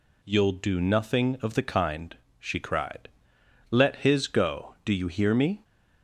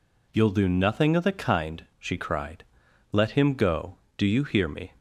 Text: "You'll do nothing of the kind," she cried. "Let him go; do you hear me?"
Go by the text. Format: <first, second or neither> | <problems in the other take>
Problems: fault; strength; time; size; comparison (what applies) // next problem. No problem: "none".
second | says "his" for "him"; at 3.9 s